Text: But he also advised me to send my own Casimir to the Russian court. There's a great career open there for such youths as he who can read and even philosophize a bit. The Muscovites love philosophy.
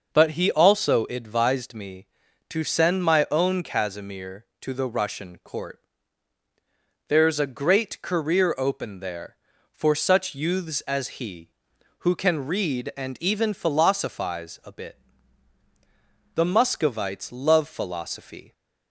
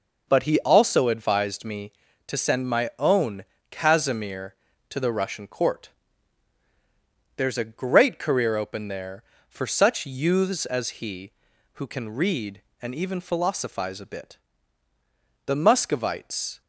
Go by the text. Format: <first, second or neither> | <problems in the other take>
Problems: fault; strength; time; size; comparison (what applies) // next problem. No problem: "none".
first | pauses between "own" and "Casimir"; slight; at 3.4 s; 0.26 s long // stops before "love philosophy"; at 16.6 s